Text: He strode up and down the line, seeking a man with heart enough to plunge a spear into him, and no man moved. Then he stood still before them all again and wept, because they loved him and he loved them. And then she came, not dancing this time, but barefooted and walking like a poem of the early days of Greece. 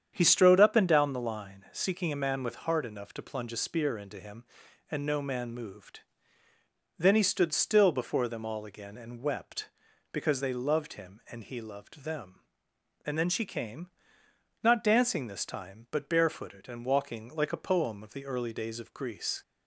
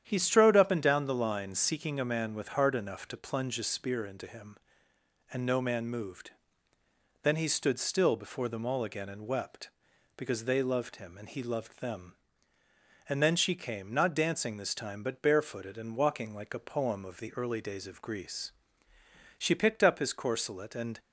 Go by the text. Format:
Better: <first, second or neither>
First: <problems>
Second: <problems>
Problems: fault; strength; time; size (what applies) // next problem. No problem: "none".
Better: first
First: starts louder than the rest; strong; until 1.1 s; 8.5 dB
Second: starts louder than the rest; strong; until 1.0 s; 9.5 dB // goes on to say "She picked up his corselet and"; from 19.3 s on; 1.6 s long